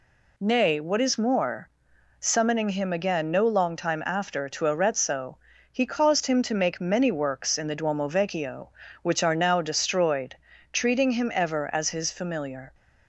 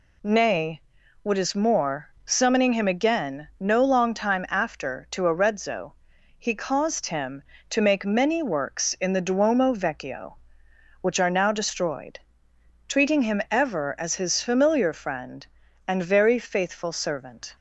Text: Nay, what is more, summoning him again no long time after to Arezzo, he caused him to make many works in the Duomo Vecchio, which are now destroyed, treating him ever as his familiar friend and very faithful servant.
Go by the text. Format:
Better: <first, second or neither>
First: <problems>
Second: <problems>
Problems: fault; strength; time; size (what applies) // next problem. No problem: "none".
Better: second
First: stops before "friend and very faithful servant"; at 12.7 s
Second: none